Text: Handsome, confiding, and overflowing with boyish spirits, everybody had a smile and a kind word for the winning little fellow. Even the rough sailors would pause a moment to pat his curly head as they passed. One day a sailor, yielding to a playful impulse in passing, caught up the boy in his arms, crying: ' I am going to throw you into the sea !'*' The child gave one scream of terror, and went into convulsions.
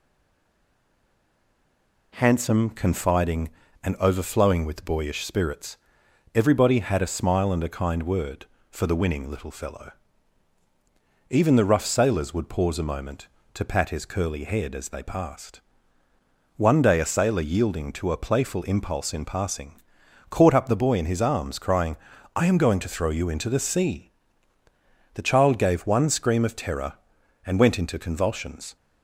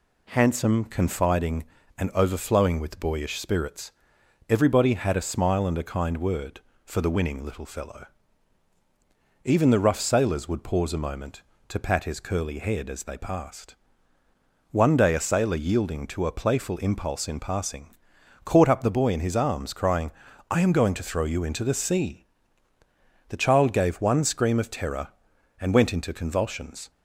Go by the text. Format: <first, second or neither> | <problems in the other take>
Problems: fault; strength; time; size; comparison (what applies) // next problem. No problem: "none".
second | stays silent before the first word; until 2.1 s; 2.1 s long